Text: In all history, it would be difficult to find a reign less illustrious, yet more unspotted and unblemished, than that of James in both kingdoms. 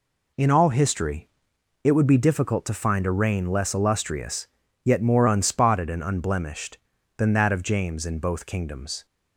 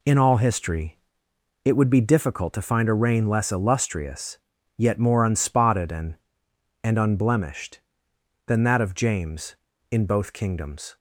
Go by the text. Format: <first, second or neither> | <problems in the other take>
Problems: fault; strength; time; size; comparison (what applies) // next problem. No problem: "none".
first | says "and" twice; at 6.8 s